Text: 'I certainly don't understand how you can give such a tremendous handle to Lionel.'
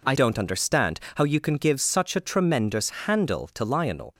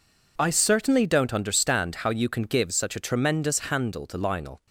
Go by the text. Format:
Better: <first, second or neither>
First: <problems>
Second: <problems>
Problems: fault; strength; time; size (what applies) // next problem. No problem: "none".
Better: second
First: skips "certainly"; at 0.1 s // pauses between "understand" and "how"; slight; at 1.0 s; 0.16 s long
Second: none